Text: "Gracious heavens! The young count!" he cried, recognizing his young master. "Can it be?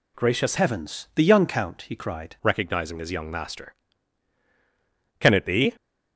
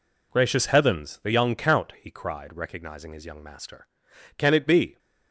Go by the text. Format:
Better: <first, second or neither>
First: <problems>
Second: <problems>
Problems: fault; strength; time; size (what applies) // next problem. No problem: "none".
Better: second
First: changes voice from "heavens" to "cried"; from 0.5 to 2.3 s; 1.8 s long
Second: none